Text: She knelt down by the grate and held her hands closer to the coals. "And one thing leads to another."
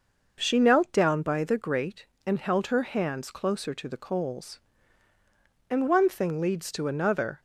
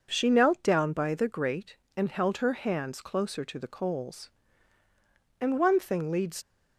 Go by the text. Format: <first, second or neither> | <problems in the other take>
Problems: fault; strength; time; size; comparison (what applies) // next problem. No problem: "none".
first | stops before "to another"; at 6.4 s